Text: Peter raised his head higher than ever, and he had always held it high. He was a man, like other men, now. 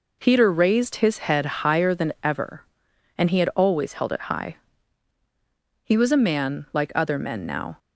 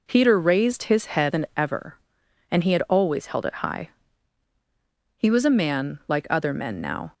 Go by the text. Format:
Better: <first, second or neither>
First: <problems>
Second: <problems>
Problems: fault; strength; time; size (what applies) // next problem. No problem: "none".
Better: first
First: none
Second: skips "higher"; at 1.3 s